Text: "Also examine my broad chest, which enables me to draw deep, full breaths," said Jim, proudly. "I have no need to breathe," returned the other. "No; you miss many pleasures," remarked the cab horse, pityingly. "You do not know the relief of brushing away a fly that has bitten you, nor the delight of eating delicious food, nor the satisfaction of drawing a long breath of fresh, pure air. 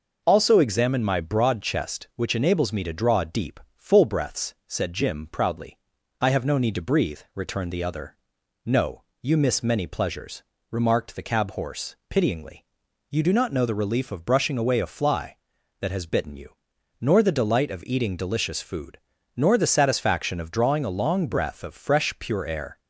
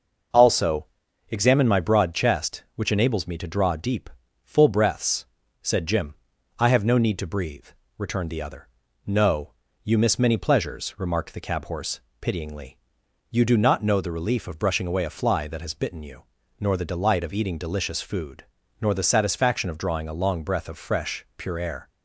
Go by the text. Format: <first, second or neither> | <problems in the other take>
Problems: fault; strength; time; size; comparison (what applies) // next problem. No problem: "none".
first | pauses between "Also" and "examine"; at 0.8 s; 0.42 s long // skips "proudly"; at 6.3 s